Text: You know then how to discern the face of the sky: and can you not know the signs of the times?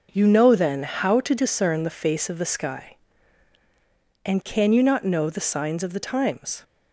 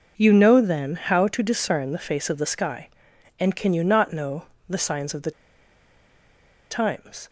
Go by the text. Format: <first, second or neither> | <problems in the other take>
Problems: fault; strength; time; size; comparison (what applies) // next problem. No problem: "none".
first | pauses between "know" and "the"; slight; at 4.4 s; 0.24 s long // pauses between "the" and "times"; strong; at 5.3 s; 1.3 s long